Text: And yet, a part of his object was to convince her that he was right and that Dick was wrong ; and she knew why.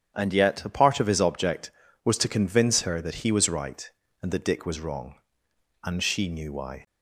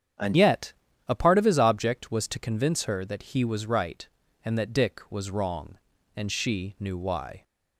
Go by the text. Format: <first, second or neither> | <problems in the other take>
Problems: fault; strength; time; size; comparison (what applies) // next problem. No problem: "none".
first | starts louder than the rest; strong; until 1.5 s; 8.5 dB; strong in the first // changes voice at "yet"; from 0.3 s on; 7.1 s long